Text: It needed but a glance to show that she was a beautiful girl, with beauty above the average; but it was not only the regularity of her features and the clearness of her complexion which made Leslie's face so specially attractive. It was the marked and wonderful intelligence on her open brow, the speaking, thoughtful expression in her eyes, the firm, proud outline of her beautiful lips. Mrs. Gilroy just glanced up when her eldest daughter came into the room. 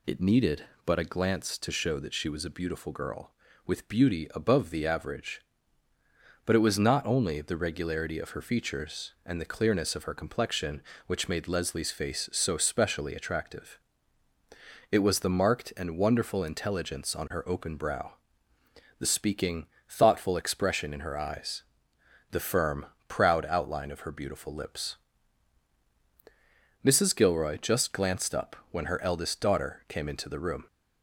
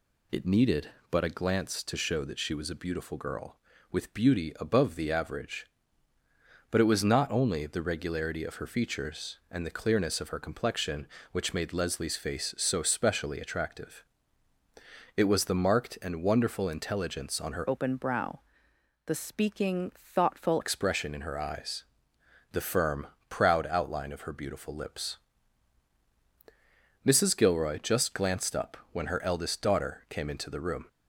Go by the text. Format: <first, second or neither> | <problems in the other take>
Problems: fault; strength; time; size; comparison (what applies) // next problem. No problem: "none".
first | changes voice from "open" to "thoughtful"; from 17.6 to 20.6 s; 3.0 s long // pauses between "up" and "when"; slight; at 28.7 s; 0.16 s long; slight in the first